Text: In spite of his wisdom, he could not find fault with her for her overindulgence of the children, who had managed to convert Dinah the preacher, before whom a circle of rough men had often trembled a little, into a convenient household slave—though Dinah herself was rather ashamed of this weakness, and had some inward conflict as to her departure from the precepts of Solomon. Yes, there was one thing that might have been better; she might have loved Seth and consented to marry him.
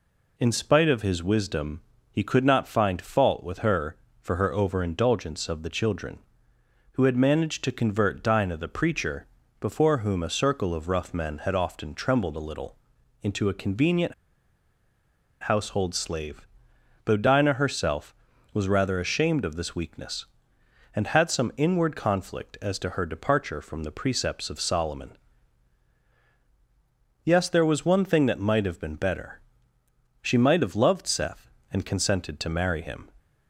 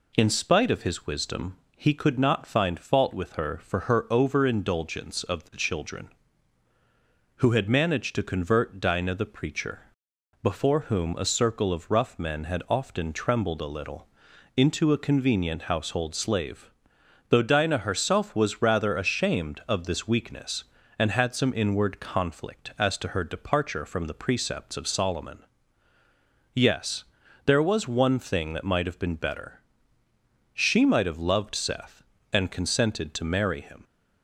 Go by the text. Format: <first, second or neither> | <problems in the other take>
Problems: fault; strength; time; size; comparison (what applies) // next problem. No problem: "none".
second | pauses between "convenient" and "household"; strong; at 14.1 s; 1.2 s long